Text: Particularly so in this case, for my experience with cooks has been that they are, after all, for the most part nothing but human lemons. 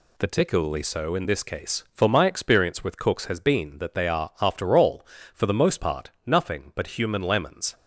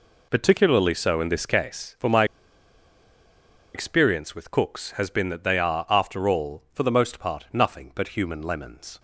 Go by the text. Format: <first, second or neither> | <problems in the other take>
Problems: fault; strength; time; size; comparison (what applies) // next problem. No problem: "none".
first | pauses between "my" and "experience"; strong; at 2.2 s; 1.5 s long